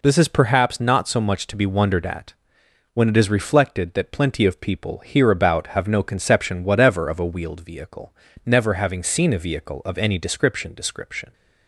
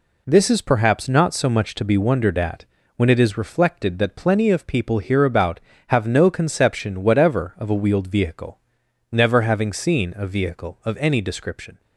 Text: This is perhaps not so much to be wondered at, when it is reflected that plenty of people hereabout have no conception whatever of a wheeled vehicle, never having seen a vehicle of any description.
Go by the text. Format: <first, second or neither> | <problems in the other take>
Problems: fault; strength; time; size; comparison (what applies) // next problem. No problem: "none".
second | says "description" twice; at 10.7 s